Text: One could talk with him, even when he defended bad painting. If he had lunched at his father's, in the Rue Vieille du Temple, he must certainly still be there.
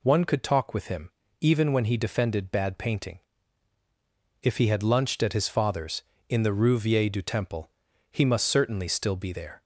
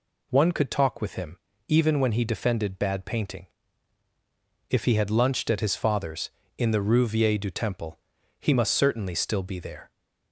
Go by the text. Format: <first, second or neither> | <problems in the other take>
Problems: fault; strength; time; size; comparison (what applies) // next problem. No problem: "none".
neither | none